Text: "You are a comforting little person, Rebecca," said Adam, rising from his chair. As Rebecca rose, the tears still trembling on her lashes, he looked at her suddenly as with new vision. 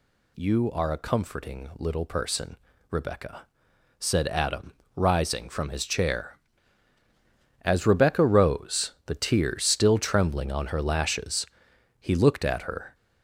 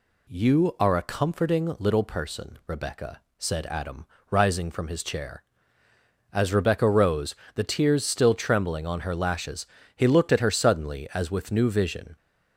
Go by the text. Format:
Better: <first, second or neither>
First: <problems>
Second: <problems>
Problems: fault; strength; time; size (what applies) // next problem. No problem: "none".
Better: second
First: stops before "suddenly as with new vision"; at 12.9 s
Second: none